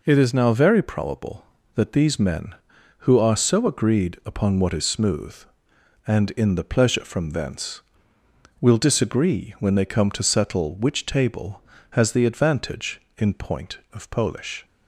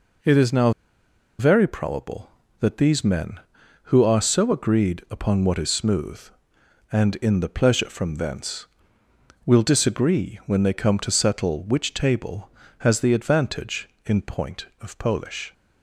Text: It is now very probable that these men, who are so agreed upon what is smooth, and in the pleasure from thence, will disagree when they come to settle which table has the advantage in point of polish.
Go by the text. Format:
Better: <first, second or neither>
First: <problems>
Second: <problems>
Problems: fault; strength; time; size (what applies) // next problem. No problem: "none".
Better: first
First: none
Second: pauses between "now" and "very"; noticeable; at 0.7 s; 0.68 s long